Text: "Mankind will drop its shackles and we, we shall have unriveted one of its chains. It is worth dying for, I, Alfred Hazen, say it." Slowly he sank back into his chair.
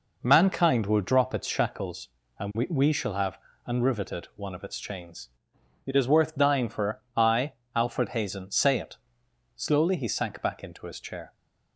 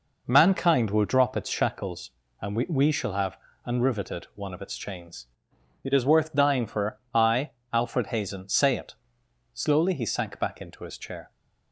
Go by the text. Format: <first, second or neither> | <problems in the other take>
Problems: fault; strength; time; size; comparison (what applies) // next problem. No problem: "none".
neither | pauses between "have" and "unriveted"; slight; the same in both